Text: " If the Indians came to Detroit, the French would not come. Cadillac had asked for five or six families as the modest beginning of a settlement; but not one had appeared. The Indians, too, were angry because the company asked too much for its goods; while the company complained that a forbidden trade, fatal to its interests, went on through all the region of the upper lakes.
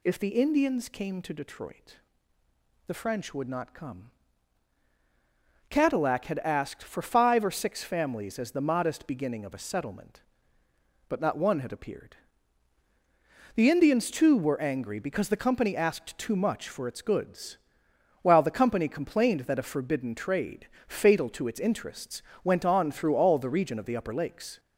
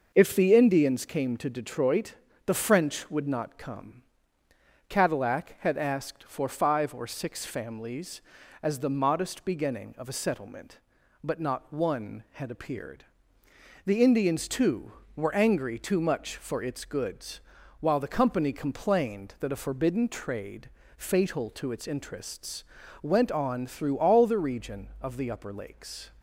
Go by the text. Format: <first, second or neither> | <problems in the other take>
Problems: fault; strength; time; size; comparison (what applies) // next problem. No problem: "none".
first | skips "because the company asked"; at 15.7 s